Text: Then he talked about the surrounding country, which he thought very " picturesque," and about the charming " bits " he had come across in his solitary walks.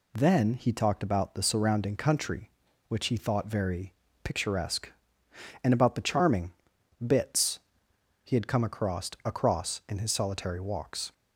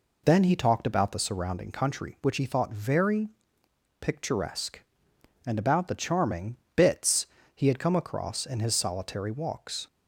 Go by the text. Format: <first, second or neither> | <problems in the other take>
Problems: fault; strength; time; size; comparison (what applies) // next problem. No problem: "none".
second | says "across" twice; at 9.2 s